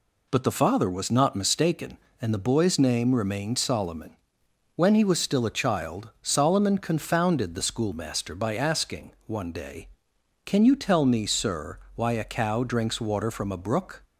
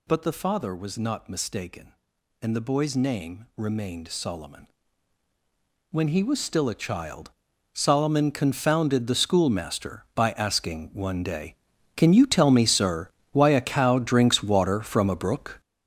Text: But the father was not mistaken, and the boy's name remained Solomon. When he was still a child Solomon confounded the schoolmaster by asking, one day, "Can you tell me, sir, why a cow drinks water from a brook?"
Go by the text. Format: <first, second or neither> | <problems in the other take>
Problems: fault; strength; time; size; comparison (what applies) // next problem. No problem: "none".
first | gets louder; strong; throughout; 9.5 dB // pauses between "child" and "Solomon"; at 7.2 s; 0.44 s long